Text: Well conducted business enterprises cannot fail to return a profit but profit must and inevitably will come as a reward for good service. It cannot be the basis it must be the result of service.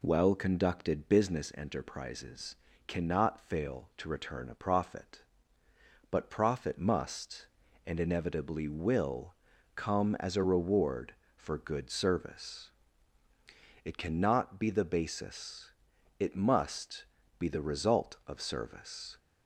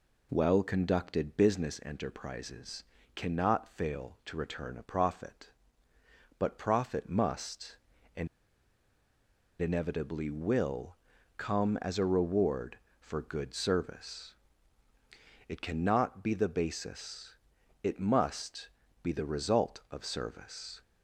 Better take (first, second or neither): first